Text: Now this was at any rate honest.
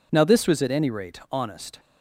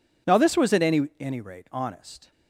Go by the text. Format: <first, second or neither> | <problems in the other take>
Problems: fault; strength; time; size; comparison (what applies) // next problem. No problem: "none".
first | says "any" twice; at 1.1 s